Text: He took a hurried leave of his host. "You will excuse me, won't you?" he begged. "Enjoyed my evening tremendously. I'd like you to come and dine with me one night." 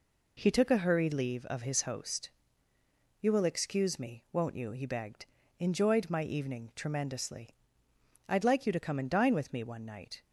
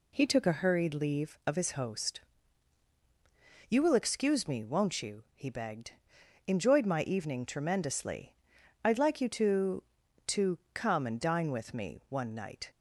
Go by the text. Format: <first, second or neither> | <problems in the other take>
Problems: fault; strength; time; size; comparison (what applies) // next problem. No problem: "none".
first | says "to" twice; at 10.2 s